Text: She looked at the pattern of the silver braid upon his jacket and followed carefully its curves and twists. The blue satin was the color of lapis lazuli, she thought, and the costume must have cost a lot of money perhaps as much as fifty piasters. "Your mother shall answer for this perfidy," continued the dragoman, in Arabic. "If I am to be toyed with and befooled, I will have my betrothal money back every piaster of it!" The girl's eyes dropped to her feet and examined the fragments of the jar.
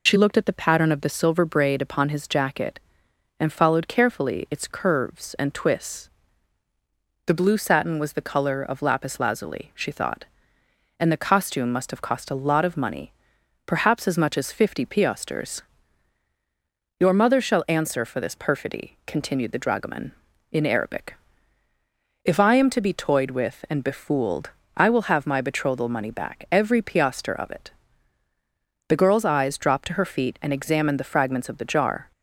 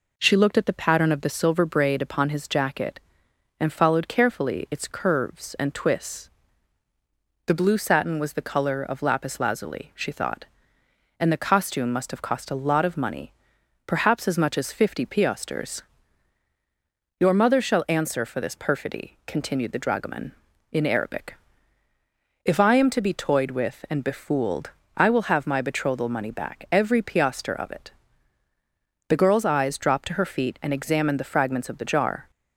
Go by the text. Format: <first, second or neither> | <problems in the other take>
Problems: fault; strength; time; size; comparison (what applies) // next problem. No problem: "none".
second | loses the start of "She"; at 0.0 s; 65 ms // pauses between "money" and "perhaps"; noticeable; at 13.1 s; 0.56 s long; noticeable in the second